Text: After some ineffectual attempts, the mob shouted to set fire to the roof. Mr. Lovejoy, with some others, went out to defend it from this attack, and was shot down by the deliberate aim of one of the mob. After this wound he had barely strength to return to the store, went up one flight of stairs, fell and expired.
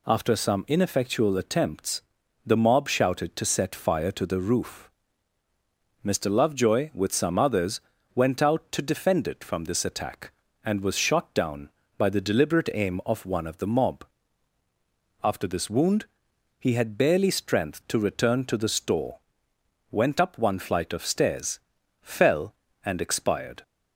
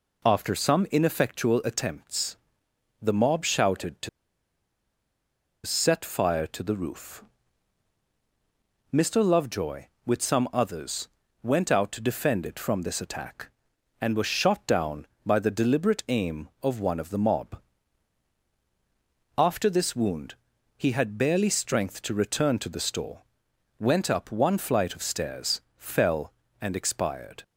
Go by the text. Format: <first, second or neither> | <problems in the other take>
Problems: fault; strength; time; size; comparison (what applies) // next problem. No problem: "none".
first | pauses between "to" and "set"; strong; at 4.0 s; 1.5 s long // pauses between "wound" and "he"; noticeable; at 20.3 s; 0.46 s long; noticeable in the first